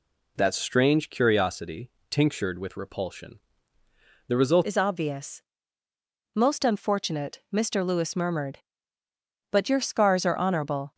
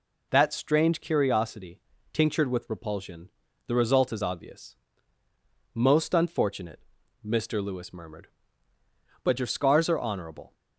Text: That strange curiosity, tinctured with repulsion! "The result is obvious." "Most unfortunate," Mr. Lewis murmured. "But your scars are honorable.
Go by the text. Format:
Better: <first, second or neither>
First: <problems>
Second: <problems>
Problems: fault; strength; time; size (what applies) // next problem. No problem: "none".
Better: second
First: changes voice at "is"; from 4.6 s on; 6.3 s long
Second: none